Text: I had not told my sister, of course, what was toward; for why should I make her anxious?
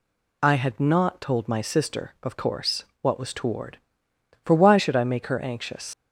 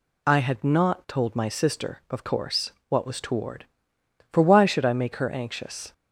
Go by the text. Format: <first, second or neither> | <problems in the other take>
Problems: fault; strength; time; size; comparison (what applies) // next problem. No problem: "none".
second | leaves "anxious" unfinished; at 5.9 s; 90 ms